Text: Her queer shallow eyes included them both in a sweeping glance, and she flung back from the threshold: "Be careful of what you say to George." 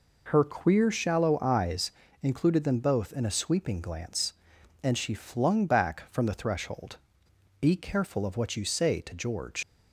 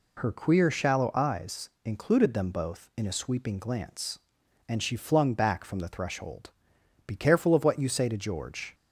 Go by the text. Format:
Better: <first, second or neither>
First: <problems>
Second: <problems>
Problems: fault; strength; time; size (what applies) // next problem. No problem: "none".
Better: second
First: pauses between "eyes" and "included"; slight; at 1.9 s; 0.28 s long // leaves "George" unfinished; at 9.6 s; 90 ms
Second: none